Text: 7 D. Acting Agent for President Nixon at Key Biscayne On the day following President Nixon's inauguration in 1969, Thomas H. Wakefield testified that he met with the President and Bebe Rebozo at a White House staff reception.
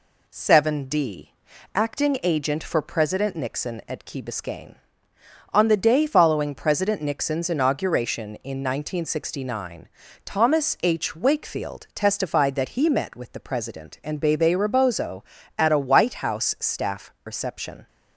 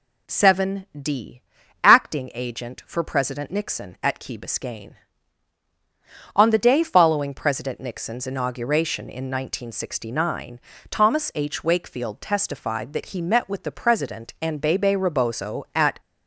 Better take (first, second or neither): first